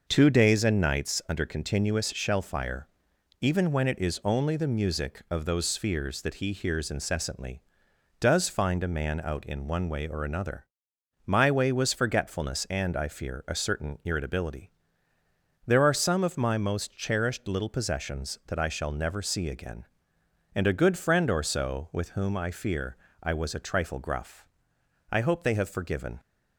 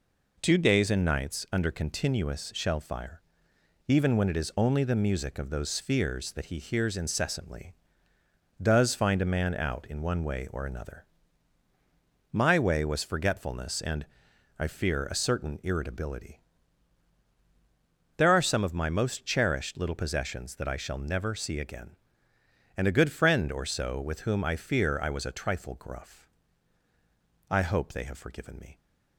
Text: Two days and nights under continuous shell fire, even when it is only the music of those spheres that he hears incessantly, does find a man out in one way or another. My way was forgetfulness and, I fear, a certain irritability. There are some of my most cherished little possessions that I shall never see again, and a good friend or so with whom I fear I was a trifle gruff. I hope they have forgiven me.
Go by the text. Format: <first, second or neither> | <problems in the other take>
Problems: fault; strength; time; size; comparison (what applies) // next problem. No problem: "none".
second | pauses between "fear" and "I"; slight; at 22.9 s; 0.26 s long // stops before "me"; at 26.1 s